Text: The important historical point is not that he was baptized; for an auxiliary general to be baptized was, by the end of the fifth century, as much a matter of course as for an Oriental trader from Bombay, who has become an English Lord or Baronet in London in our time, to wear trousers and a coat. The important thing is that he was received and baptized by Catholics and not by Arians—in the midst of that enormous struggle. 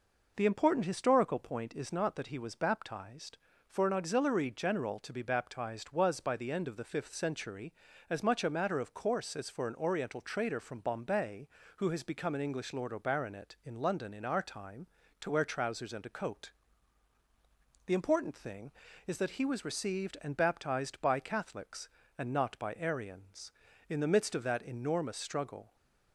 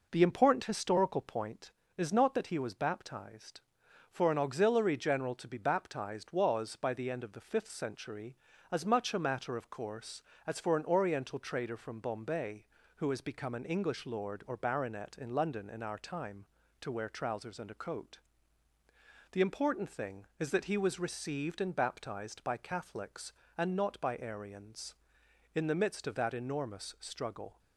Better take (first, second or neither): neither